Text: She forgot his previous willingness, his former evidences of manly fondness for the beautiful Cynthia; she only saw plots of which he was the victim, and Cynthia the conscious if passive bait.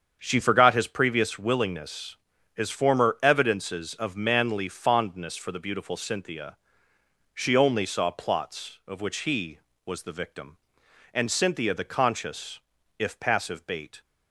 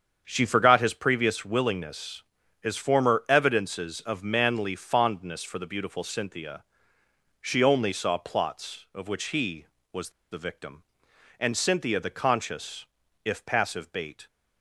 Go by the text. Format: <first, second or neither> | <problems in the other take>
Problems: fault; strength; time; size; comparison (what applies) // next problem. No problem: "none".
first | starts louder than the rest; strong; until 1.2 s; 7.5 dB; strong in the first // pauses between "was" and "the"; slight; at 10.0 s; 0.21 s long // pauses between "conscious" and "if"; at 12.8 s; 0.40 s long; also in the first